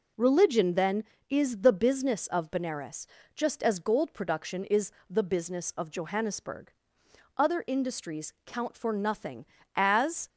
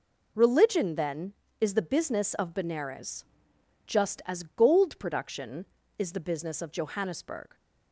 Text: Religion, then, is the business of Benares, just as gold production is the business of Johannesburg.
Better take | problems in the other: second | pauses between "is" and "the"; slight; at 4.9 s; 0.18 s long // goes on to say "Other industries count for nothing as"; strong; from 7.3 s on; 2.9 s long

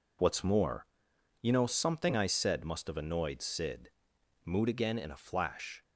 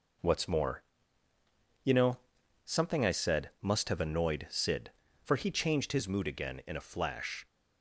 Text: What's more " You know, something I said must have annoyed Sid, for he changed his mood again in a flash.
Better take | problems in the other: second | skips "for he changed his"; at 4.1 s

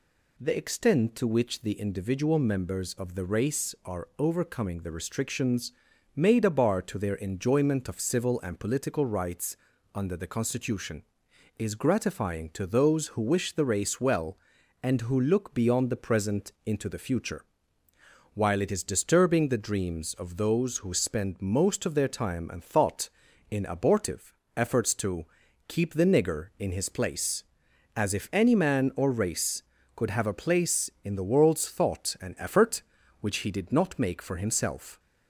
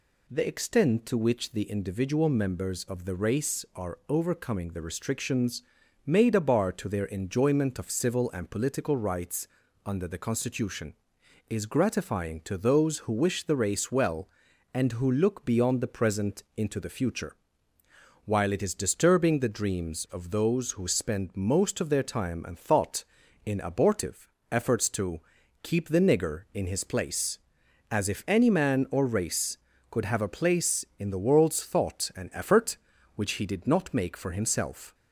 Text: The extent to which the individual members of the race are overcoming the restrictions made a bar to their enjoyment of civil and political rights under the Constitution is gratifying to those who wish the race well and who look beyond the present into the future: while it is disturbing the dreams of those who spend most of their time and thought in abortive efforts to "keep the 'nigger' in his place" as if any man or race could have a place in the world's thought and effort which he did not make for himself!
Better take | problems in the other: neither | pauses between "restrictions" and "made"; the same in both // pauses between "rights" and "under"; the same in both // pauses between "abortive" and "efforts"; slight; the same in both // pauses between "to" and "keep"; the same in both

